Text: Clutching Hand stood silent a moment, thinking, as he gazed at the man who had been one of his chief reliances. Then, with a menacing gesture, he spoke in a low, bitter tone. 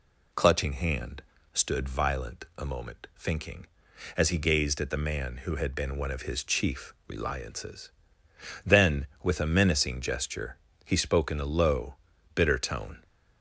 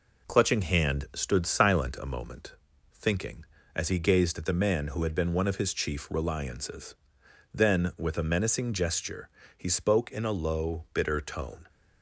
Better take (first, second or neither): second